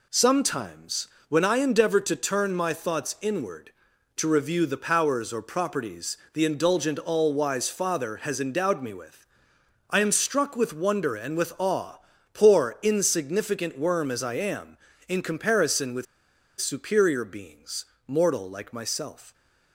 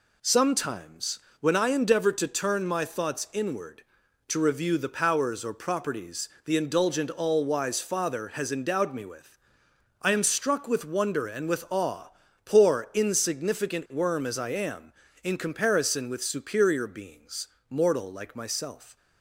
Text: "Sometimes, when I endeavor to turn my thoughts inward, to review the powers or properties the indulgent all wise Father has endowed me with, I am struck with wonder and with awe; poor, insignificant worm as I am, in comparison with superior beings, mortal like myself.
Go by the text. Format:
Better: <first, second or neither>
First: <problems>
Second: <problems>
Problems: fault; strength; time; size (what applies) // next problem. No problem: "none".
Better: second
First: pauses between "properties" and "the"; slight; at 6.1 s; 0.16 s long // pauses between "with" and "superior"; noticeable; at 16.0 s; 0.55 s long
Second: pauses between "properties" and "the"; slight; at 6.2 s; 0.16 s long